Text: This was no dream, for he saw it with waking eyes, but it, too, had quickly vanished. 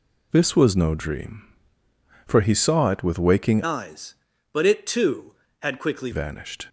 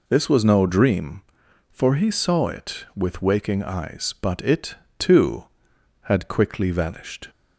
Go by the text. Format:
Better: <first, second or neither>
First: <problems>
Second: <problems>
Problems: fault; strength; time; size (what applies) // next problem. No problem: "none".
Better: second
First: changes voice from "eyes" to "quickly"; from 3.6 to 6.1 s; 2.5 s long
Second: none